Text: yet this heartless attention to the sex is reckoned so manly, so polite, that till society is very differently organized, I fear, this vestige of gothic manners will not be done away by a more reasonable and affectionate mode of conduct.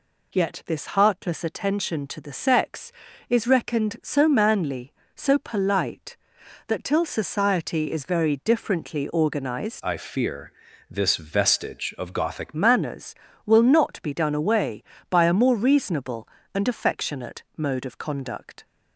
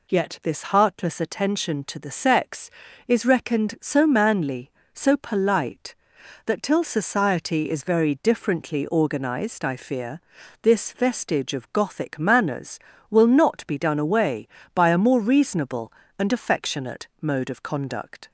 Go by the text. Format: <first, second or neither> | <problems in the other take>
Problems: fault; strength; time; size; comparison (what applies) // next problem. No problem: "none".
second | changes voice from "I" to "gothic"; from 9.8 to 12.5 s; 2.7 s long